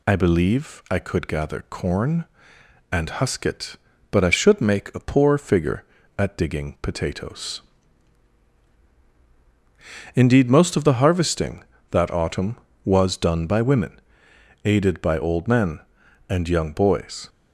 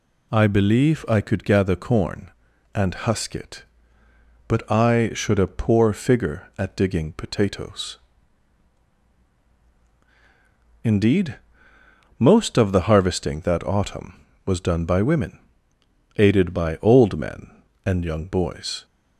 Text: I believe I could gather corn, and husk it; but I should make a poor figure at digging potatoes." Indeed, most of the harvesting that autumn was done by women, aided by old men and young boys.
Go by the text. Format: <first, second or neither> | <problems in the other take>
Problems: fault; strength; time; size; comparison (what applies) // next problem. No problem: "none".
first | skips "make"; at 5.3 s